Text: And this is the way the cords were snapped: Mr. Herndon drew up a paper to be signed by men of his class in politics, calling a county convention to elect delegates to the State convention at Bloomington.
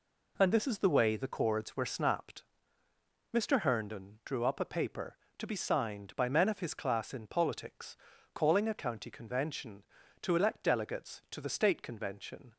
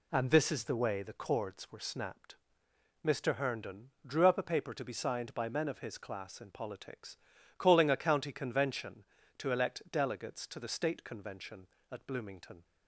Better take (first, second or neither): second